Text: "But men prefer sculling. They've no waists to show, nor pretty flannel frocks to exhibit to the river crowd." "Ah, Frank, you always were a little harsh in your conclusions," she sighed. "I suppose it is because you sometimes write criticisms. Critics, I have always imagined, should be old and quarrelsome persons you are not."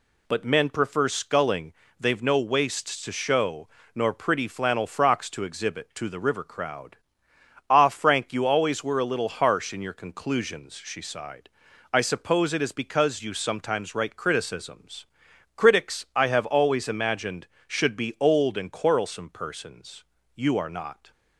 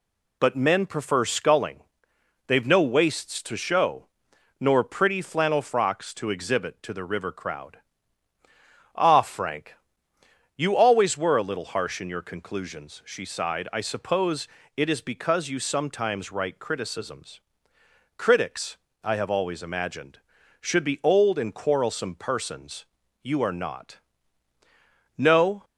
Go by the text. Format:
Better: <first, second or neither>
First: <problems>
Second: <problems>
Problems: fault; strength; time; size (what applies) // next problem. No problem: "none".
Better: first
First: pauses between "persons" and "you"; slight; at 20.0 s; 0.30 s long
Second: pauses between "suppose" and "it"; slight; at 14.4 s; 0.30 s long // pauses between "persons" and "you"; at 22.8 s; 0.38 s long // goes on to say "No"; slight; from 25.1 s on; 0.48 s long